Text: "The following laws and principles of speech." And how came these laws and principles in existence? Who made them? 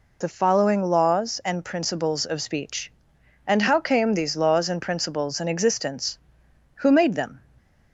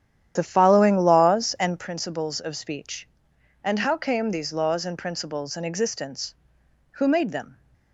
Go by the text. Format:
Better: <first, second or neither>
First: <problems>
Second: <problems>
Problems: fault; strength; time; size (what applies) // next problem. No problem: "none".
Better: first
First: none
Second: starts louder than the rest; strong; until 1.9 s; 10.5 dB